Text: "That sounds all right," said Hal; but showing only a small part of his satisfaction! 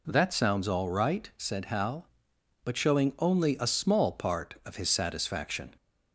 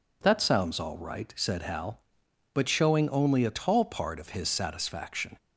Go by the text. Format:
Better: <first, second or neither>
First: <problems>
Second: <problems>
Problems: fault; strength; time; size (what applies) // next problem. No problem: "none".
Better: first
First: none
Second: says "tall" for "small"; at 3.4 s